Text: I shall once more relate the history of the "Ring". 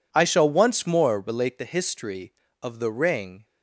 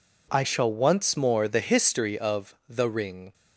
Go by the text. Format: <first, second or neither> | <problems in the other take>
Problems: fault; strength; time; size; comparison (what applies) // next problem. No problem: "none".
first | skips "relate"; at 1.4 s // pauses between "of" and "the"; slight; at 2.5 s; 0.16 s long